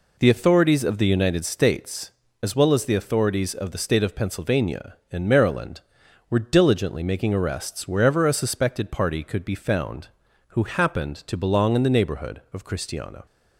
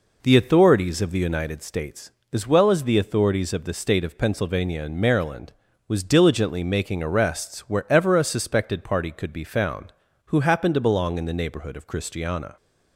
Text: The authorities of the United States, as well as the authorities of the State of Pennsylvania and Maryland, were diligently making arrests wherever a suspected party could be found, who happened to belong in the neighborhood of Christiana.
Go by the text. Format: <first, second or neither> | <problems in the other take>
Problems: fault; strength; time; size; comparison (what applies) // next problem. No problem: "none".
first | says "was" for "were"; at 5.8 s